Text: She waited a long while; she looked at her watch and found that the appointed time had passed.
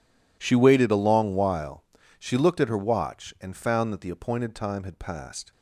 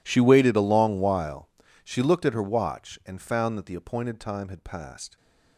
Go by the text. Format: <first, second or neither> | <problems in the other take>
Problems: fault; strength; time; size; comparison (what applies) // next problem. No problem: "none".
first | gets quieter; strong; throughout; 22.5 dB